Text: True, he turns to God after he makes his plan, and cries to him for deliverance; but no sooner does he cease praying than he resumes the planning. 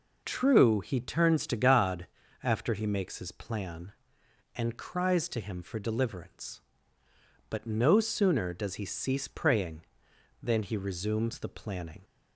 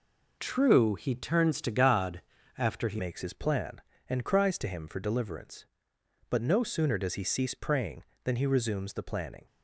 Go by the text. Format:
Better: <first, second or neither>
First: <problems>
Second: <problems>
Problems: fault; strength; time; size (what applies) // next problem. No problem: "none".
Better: first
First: pauses between "God" and "after"; slight; at 2.0 s; 0.34 s long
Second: pauses between "God" and "after"; slight; at 2.2 s; 0.34 s long // changes voice at "makes"; from 2.9 s on; 6.5 s long